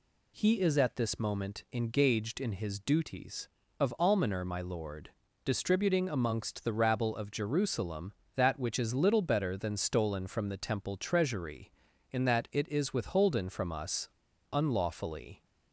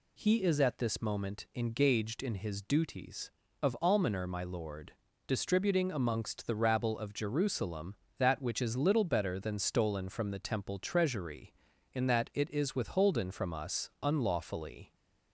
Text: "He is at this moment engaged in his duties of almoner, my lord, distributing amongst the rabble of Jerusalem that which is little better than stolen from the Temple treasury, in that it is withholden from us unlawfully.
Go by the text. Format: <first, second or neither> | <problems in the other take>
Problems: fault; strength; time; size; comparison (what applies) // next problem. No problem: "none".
second | pauses between "us" and "unlawfully"; at 14.0 s; 0.43 s long